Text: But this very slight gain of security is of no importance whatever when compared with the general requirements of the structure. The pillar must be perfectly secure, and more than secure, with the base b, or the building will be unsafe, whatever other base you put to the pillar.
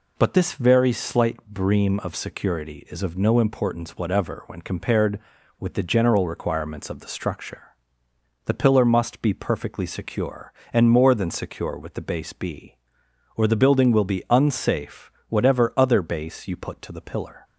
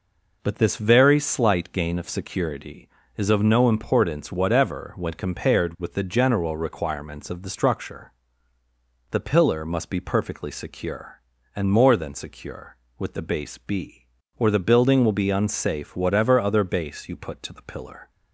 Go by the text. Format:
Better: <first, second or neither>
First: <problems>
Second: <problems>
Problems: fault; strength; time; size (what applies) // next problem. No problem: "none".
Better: second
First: says "bream" for "gain"; at 1.4 s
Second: none